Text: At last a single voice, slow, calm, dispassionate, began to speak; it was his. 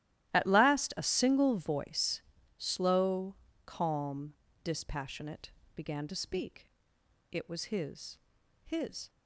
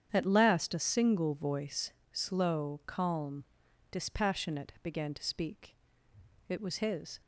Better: second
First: starts louder than the rest; strong; until 1.3 s; 14 dB // says "his" twice; at 8.6 s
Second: starts louder than the rest; strong; until 1.1 s; 8.5 dB

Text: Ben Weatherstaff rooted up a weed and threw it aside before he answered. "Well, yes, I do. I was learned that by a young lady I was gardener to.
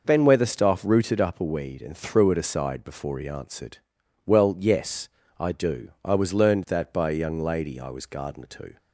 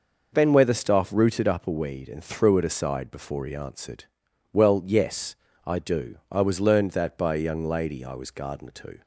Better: neither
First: none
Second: none

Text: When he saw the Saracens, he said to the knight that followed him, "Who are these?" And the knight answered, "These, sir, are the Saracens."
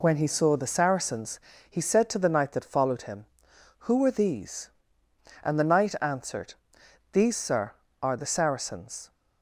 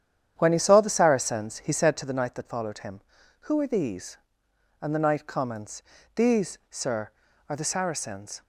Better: first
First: none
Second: starts louder than the rest; strong; until 1.3 s; 9.5 dB // says "comments" for "answered"; at 5.2 s

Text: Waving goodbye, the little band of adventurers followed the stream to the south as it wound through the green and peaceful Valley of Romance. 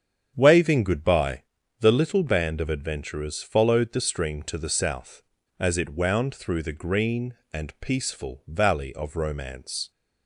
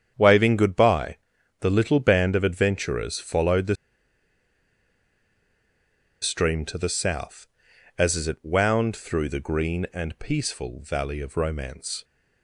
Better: first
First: starts louder than the rest; strong; until 1.3 s; 8 dB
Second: starts louder than the rest; strong; until 1.1 s; 8.5 dB // pauses between "the" and "stream"; strong; at 3.7 s; 2.4 s long

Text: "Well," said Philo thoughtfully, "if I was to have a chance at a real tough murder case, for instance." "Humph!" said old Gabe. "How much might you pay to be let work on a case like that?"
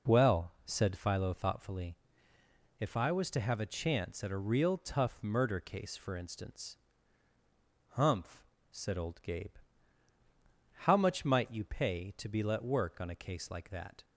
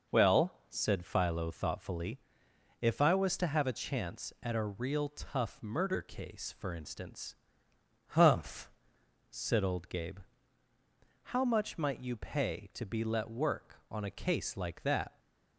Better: neither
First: none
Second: none

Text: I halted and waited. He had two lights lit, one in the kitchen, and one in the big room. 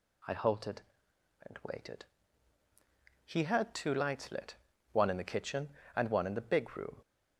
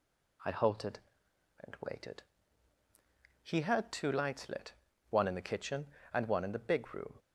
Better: second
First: gets louder; slight; throughout; 2.5 dB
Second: none

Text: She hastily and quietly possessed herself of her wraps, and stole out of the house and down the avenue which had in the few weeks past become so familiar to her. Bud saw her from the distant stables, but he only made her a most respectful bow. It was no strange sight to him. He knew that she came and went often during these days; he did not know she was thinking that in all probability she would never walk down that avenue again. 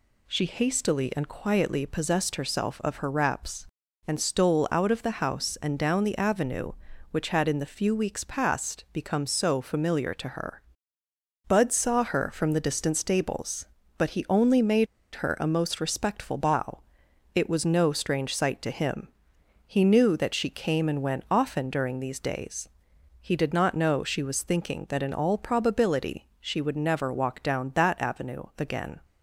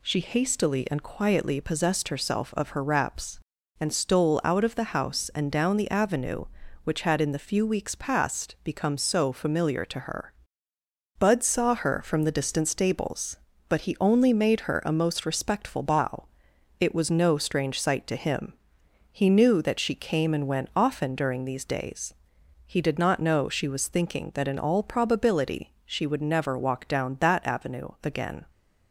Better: second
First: pauses between "made" and "her"; slight; at 14.8 s; 0.28 s long // pauses between "avenue" and "again"; slight; at 28.4 s; 0.16 s long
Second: pauses between "avenue" and "again"; slight; at 27.8 s; 0.16 s long

